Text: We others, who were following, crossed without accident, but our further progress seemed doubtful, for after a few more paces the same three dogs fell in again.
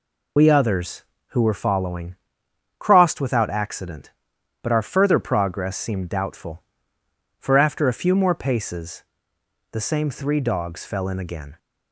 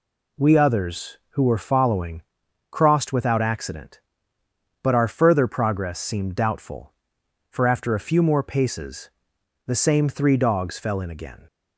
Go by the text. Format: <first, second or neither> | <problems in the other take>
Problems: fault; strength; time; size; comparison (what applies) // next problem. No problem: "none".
second | loses the start of "We"; at 0.3 s; 55 ms // pauses between "paces" and "the"; noticeable; at 9.0 s; 0.68 s long; noticeable in the second